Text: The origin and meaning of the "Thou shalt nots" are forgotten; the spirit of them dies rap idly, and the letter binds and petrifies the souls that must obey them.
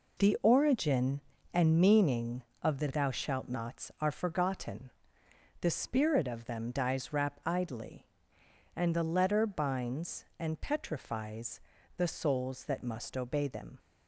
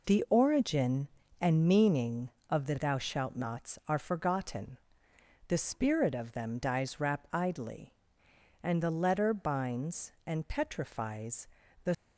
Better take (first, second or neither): first